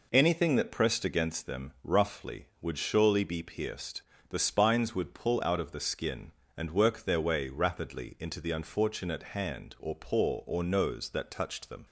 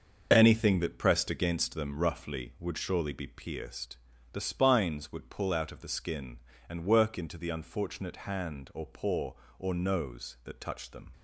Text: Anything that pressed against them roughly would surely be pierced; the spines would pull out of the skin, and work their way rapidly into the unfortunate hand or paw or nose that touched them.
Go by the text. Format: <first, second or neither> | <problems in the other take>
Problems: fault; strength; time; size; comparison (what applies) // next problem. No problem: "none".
first | starts louder than the rest; until 1.3 s; 6.5 dB // skips "their way rapidly"; at 7.1 s